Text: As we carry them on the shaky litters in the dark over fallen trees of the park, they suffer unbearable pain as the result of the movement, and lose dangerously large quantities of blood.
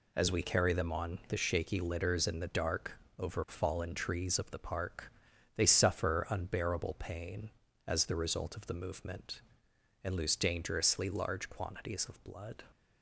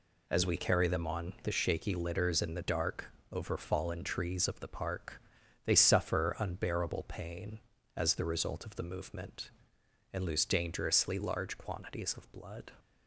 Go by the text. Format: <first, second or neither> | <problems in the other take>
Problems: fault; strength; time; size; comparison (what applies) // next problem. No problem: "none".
neither | pauses between "dark" and "over"; slight; the same in both